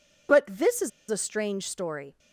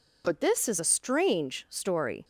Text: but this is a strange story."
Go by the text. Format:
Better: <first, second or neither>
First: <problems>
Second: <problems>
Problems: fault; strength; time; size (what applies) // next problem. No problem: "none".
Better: second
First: pauses between "is" and "a"; slight; at 0.9 s; 0.20 s long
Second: none